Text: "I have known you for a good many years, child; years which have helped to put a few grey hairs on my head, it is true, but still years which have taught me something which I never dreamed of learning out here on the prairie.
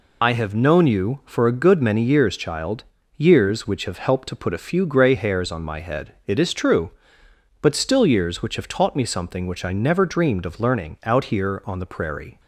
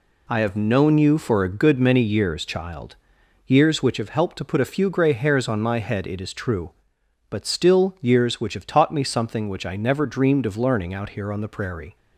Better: second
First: loses the start of "I"; at 0.2 s; 45 ms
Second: none

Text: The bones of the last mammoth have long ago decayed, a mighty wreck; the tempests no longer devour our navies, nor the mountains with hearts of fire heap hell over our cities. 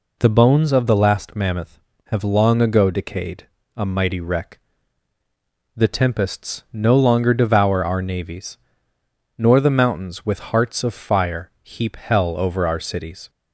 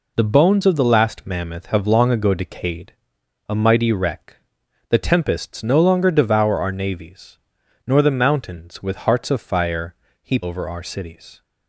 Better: first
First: none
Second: pauses between "fire" and "heap"; slight; at 9.9 s; 0.26 s long // skips "hell"; at 10.4 s

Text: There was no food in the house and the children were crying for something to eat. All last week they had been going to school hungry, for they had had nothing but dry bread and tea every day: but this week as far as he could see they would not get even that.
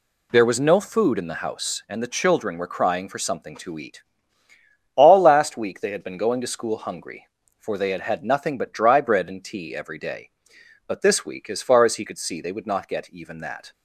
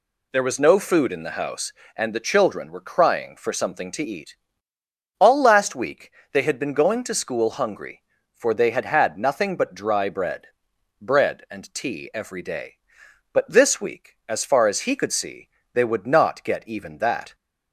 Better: first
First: none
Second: pauses between "week" and "they"; slight; at 6.1 s; 0.22 s long // says "bread" twice; at 10.9 s // pauses between "see" and "they"; slight; at 15.4 s; 0.28 s long

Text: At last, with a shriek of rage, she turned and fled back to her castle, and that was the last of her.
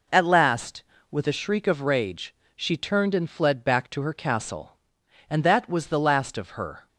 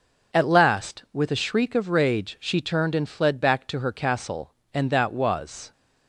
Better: first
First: none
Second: stops before "the last of her"; at 5.7 s

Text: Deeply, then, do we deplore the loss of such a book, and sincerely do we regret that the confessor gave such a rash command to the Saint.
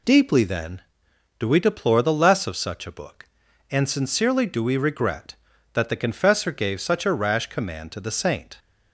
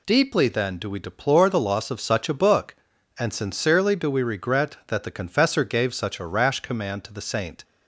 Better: second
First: says "less" for "loss"; at 2.1 s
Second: none

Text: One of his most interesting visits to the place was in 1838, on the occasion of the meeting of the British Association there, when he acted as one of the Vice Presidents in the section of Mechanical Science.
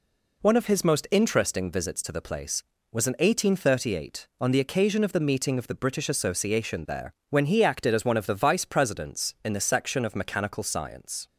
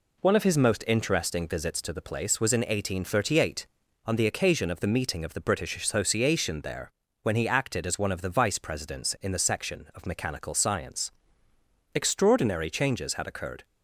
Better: first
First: none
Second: goes on to say "Extraordinary changes had occurred"; strong; from 11.9 s on; 1.6 s long

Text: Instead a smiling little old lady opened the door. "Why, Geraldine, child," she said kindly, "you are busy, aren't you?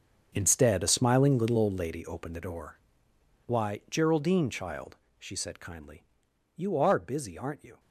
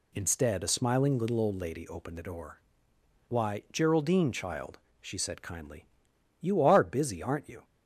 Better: second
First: gets quieter; strong; throughout; 14 dB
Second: none

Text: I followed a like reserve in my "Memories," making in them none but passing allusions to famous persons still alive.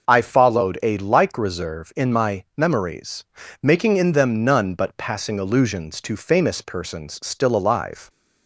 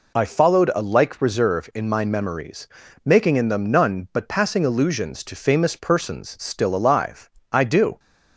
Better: first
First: none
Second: goes on to say "I do"; slight; from 7.5 s on; 0.48 s long

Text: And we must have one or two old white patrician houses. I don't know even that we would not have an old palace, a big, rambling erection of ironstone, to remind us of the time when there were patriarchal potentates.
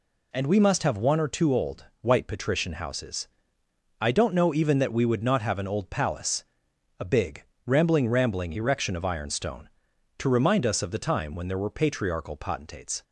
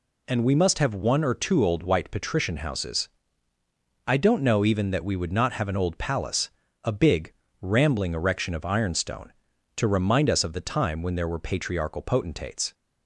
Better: second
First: pauses between "old" and "white"; slight; at 1.8 s; 0.16 s long // says "rambling" twice; at 8.0 s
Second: none

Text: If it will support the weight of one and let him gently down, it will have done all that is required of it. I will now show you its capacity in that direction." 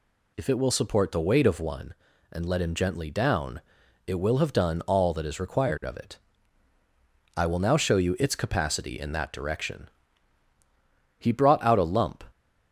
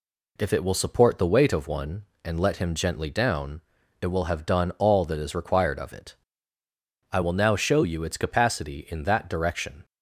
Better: second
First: goes on to say "He brought out a lump"; noticeable; from 11.1 s on; 1.0 s long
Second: none

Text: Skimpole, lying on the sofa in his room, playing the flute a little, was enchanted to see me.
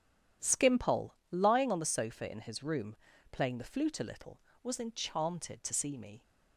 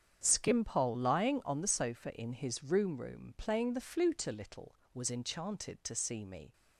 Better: first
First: none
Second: starts louder than the rest; strong; until 1.2 s; 8 dB // says "room" twice; at 3.0 s

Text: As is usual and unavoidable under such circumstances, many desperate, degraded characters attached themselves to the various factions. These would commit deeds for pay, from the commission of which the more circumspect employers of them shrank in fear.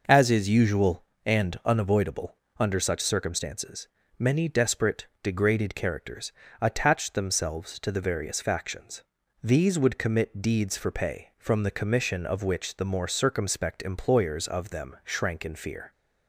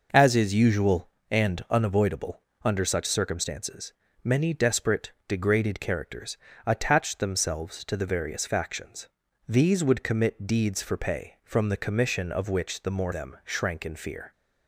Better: first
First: pauses between "unavoidable" and "under"; slight; at 2.3 s; 0.24 s long // pauses between "characters" and "attached"; slight; at 6.3 s; 0.30 s long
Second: pauses between "unavoidable" and "under"; slight; at 2.4 s; 0.24 s long // pauses between "characters" and "attached"; slight; at 6.3 s; 0.30 s long // skips "circumspect employers of"; at 13.1 s

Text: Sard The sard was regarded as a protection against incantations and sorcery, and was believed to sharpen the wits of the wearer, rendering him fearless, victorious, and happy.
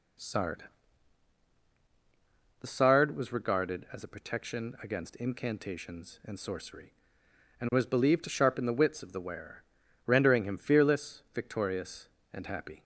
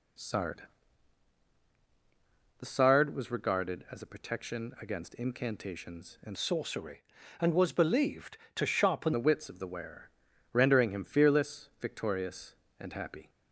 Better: first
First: pauses between "Sard" and "The"; strong; at 0.6 s; 1.9 s long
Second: pauses between "Sard" and "The"; strong; at 0.6 s; 1.9 s long // changes voice from "sorcery" to "sharpen"; from 6.3 to 9.1 s; 2.8 s long

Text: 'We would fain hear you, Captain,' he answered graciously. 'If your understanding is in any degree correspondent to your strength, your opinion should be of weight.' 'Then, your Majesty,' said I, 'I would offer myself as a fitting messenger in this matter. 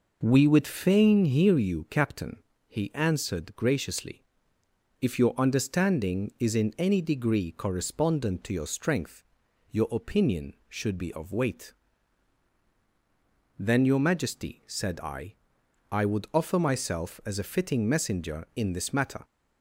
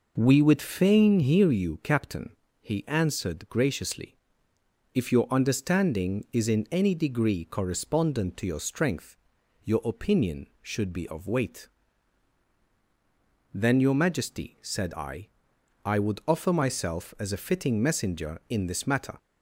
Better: neither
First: none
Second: none

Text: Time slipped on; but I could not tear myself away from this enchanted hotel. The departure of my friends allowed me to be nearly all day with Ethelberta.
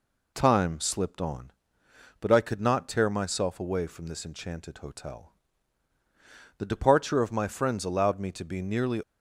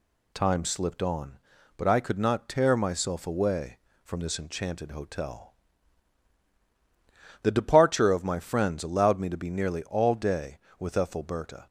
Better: second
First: stops before "all day with Ethelberta"; at 9.0 s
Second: none

